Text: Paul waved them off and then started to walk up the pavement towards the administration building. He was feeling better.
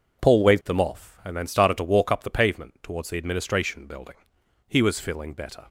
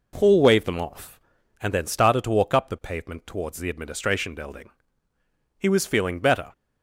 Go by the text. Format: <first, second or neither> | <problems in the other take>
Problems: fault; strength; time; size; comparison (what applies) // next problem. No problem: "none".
neither | none